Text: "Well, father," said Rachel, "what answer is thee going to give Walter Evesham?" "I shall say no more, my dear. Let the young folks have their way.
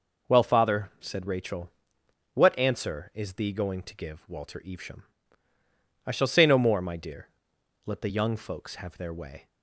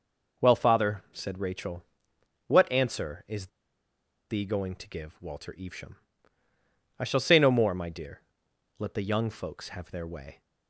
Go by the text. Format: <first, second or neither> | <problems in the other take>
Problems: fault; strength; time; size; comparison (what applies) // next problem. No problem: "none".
first | pauses between "is" and "thee"; noticeable; at 3.4 s; 0.82 s long